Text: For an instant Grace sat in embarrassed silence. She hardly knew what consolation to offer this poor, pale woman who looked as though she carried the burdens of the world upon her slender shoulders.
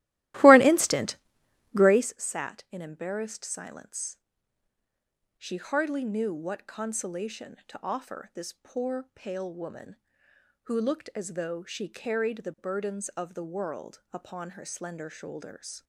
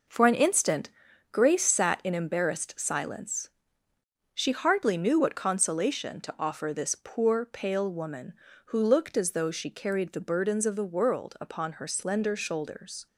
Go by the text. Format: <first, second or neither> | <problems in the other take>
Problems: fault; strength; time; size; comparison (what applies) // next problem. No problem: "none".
second | starts louder than the rest; strong; until 2.2 s; 16 dB // pauses between "instant" and "Grace"; noticeable; at 1.1 s; 0.58 s long; also in the second